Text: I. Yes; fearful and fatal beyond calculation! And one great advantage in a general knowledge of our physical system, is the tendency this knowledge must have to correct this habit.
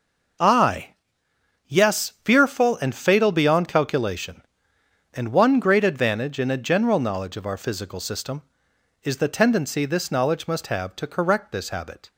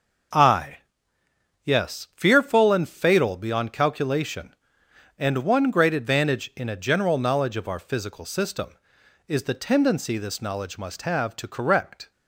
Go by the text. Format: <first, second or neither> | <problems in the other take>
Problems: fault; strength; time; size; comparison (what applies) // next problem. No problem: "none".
first | stops before "this habit"; at 12.1 s